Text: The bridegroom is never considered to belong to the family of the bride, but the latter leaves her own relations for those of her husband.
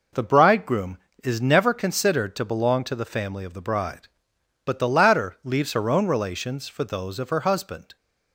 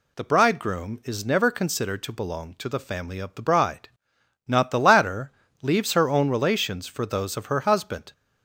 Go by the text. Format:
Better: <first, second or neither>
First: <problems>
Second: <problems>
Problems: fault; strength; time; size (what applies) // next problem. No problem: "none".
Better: first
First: none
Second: says "not" for "but"; at 4.4 s // pauses between "latter" and "leaves"; slight; at 5.3 s; 0.28 s long